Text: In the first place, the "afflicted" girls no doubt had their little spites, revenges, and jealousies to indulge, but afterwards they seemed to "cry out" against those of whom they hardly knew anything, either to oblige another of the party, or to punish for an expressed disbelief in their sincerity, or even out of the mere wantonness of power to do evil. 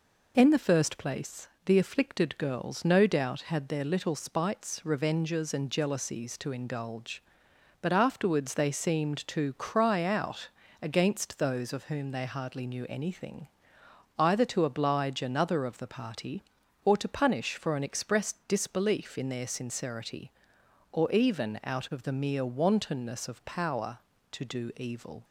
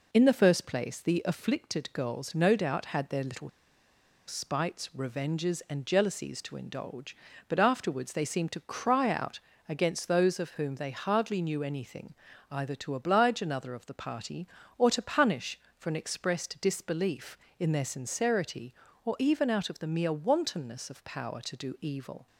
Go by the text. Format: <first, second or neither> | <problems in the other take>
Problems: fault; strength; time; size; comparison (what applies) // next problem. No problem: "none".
first | pauses between "little" and "spites"; noticeable; at 3.4 s; 0.78 s long // pauses between "out" and "against"; slight; at 9.3 s; 0.28 s long; slight in the first